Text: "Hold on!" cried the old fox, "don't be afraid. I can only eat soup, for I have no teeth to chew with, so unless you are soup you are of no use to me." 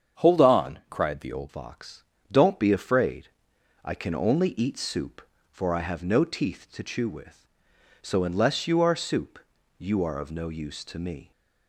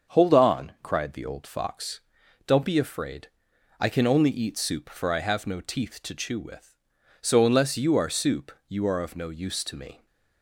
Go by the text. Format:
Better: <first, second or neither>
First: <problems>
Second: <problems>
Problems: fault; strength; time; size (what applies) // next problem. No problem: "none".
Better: second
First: starts louder than the rest; strong; until 1.3 s; 7.5 dB // changes voice at "fox"; from 1.4 s on; 9.9 s long // pauses between "soup" and "you"; at 9.3 s; 0.38 s long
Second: starts louder than the rest; until 1.2 s; 6.5 dB // pauses between "soup" and "you"; slight; at 8.5 s; 0.19 s long